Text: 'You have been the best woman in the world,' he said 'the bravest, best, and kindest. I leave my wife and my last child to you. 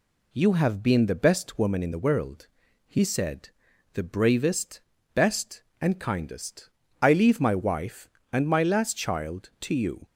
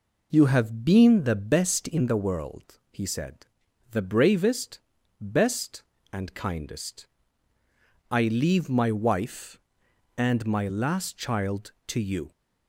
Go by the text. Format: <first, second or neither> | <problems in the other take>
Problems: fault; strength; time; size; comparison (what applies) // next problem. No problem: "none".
first | skips "woman"; at 1.8 s // pauses between "said" and "the"; at 3.4 s; 0.44 s long; also in the first